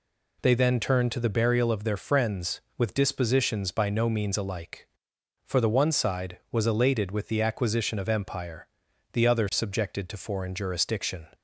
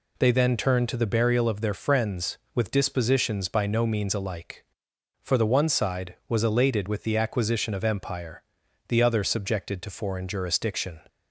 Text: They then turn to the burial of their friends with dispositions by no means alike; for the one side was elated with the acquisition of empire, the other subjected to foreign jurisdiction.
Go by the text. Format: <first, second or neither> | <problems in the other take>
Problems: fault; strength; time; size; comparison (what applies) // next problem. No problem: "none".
neither | none